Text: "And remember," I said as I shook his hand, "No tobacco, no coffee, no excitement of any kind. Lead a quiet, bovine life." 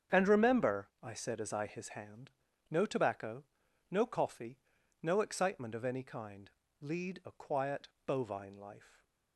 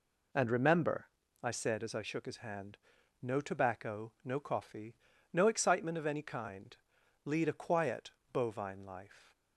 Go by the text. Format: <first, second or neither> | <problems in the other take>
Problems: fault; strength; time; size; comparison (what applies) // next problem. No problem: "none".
second | starts louder than the rest; strong; until 1.2 s; 8 dB // skips "shook"; at 1.6 s